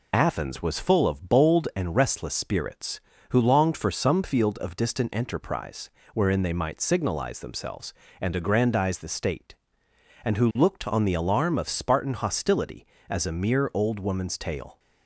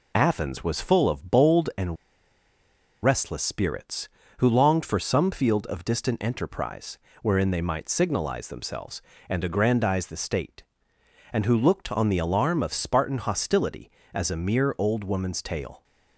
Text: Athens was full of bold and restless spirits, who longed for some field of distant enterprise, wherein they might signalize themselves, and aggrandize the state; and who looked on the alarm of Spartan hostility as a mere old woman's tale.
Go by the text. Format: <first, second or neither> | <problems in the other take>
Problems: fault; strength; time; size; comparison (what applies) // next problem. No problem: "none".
first | pauses between "and" and "restless"; at 1.9 s; 1.0 s long